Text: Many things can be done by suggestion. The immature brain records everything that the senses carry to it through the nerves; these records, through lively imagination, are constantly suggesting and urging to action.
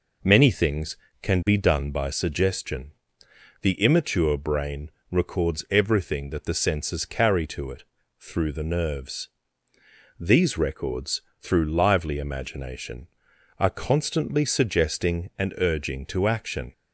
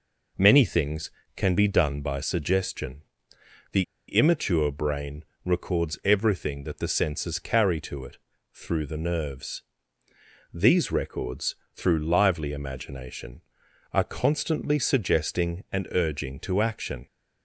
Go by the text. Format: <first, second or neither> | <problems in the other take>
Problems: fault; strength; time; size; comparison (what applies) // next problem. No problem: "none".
first | pauses between "The" and "immature"; slight; at 3.8 s; 0.25 s long // pauses between "brain" and "records"; slight; at 5.2 s; 0.20 s long; slight in the first // pauses between "it" and "through"; slight; at 8.1 s; 0.34 s long; slight in the first